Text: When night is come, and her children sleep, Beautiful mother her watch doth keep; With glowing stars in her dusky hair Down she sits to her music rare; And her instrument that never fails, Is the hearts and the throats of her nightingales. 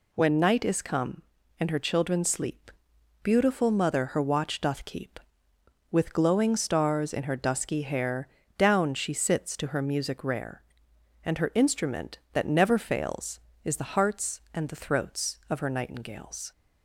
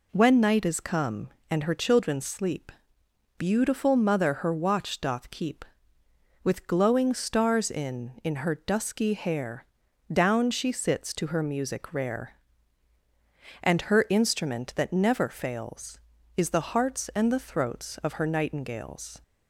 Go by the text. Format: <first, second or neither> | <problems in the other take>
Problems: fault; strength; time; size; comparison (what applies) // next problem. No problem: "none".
first | says "in" twice; at 8.2 s // pauses between "hair" and "Down"; noticeable; at 9.6 s; 0.46 s long; slight in the first